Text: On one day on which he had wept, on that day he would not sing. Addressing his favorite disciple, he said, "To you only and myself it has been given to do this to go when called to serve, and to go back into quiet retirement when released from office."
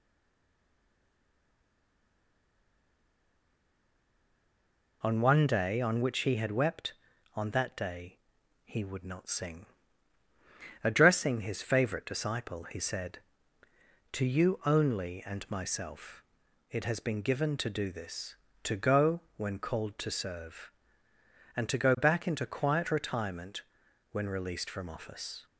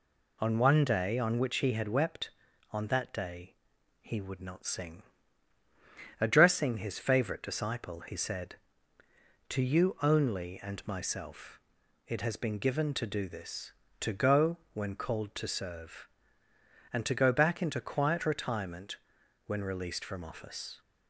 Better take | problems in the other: second | stays silent before the first word; strong; until 5.0 s; 5.0 s long // pauses between "day" and "he"; noticeable; at 8.1 s; 0.46 s long; noticeable in the second // pauses between "myself" and "it"; noticeable; at 16.2 s; 0.48 s long; noticeable in the second // pauses between "retirement" and "when"; noticeable; at 23.6 s; 0.50 s long; noticeable in the second

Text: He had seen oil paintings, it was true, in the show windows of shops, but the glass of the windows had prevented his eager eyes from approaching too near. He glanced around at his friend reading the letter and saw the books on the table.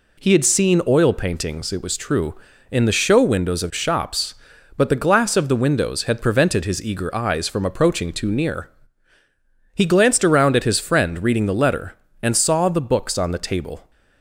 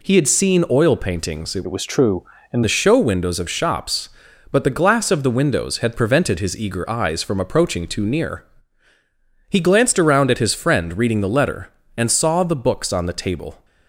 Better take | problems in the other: first | changes voice from "was" to "in"; from 1.6 to 2.6 s; 1.0 s long

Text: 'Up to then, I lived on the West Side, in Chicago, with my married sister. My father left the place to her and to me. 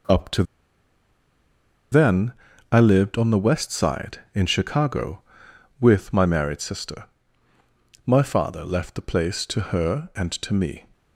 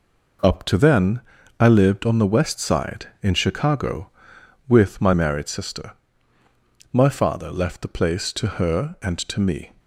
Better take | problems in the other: second | pauses between "to" and "then"; strong; at 0.4 s; 1.4 s long

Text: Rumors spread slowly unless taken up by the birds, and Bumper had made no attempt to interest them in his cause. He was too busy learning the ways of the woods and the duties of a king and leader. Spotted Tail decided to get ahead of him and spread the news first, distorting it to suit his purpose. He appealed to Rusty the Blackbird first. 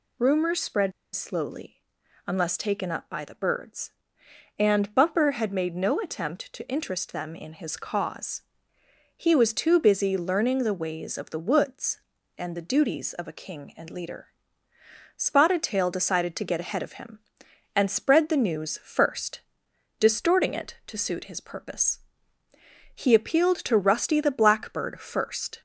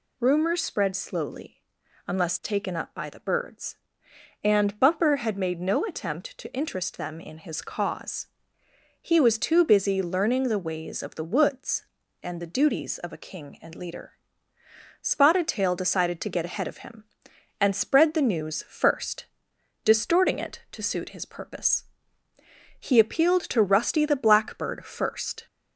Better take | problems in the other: second | pauses between "spread" and "slowly"; slight; at 0.9 s; 0.23 s long // pauses between "slowly" and "unless"; noticeable; at 1.8 s; 0.46 s long; noticeable in the second

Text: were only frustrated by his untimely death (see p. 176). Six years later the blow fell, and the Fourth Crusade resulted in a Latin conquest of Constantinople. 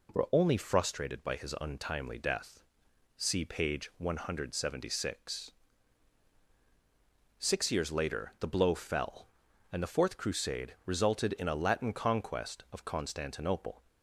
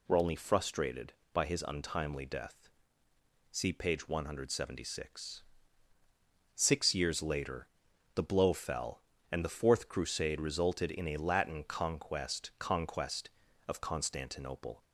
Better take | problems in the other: first | pauses between "later" and "the"; noticeable; at 7.6 s; 0.46 s long // says "conquest" twice; at 12.5 s

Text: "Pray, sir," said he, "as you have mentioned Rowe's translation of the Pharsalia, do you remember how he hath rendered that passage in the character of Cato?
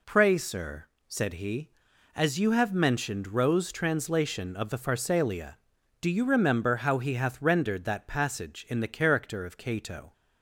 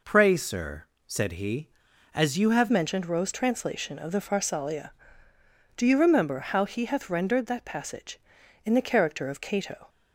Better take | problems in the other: first | changes voice at "mentioned"; from 2.7 s on; 7.1 s long

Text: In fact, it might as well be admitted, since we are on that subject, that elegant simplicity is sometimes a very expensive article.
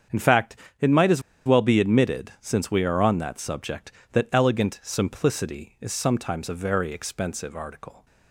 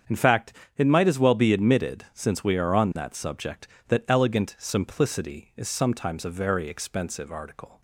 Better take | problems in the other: second | starts louder than the rest; strong; until 1.6 s; 8 dB; strong in the second // pauses between "as" and "well"; slight; at 1.2 s; 0.24 s long

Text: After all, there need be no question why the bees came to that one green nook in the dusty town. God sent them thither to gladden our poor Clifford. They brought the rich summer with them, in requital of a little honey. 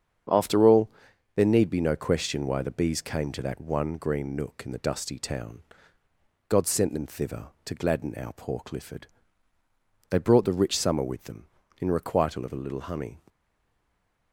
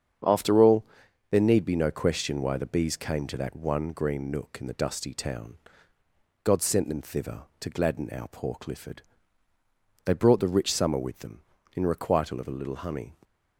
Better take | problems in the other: second | starts louder than the rest; strong; until 1.7 s; 7.5 dB; strong in the second // stays silent after the last word; from 13.2 s on; 1.1 s long

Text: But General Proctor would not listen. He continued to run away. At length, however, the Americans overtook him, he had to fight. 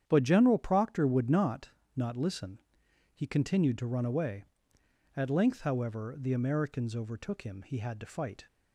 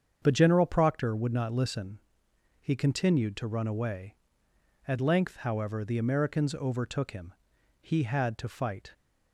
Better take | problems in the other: second | starts louder than the rest; strong; until 1.0 s; 9 dB; strong in the second // says "not" twice; at 1.9 s

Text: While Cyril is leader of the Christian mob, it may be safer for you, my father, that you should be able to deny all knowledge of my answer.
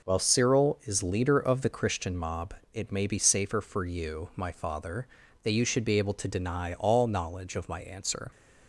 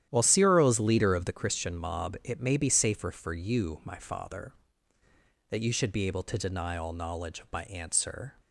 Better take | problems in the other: first | gets quieter; strong; throughout; 11.5 dB

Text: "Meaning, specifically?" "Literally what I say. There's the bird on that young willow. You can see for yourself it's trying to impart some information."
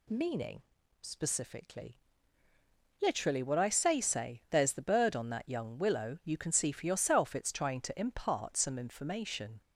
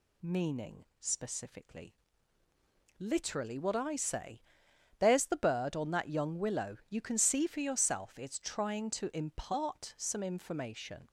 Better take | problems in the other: second | says "say" twice; at 4.0 s

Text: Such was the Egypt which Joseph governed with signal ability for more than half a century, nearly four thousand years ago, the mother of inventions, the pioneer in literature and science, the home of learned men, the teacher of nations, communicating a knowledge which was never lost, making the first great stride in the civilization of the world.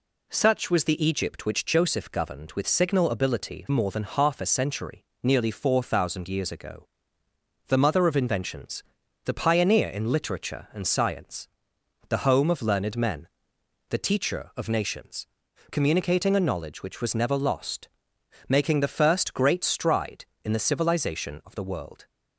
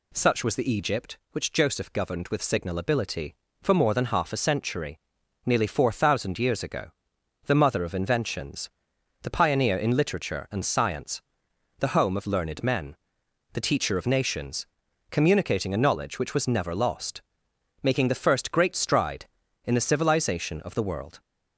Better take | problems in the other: second | skips "for"; at 3.6 s

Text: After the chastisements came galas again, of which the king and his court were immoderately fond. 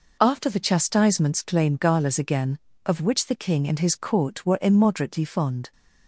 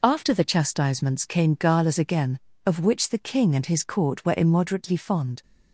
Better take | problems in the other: second | says "claim" for "came"; at 1.4 s

